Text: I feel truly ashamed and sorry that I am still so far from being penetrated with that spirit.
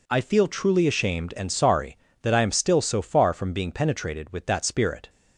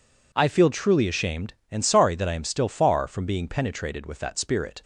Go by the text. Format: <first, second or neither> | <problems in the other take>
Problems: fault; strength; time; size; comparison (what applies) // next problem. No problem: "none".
first | skips "so"; at 2.6 s